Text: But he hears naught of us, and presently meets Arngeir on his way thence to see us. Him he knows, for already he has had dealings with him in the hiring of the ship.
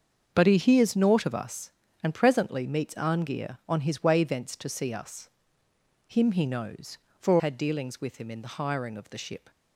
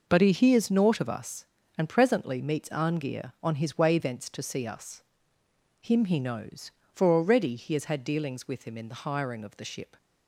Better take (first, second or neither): second